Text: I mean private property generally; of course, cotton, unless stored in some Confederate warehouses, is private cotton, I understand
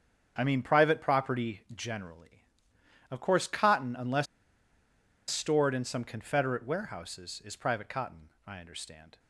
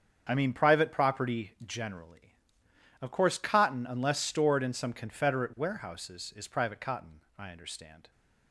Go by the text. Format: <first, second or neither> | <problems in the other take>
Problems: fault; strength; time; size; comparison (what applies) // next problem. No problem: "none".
second | starts louder than the rest; strong; until 1.3 s; 7.5 dB; strong in the second // pauses between "unless" and "stored"; at 4.2 s; 1.0 s long